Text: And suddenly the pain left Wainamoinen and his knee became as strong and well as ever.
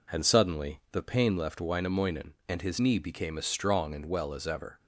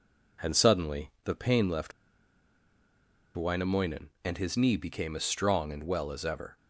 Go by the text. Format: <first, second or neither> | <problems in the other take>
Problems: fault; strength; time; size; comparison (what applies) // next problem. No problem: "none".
first | pauses between "left" and "Wainamoinen"; strong; at 1.9 s; 1.4 s long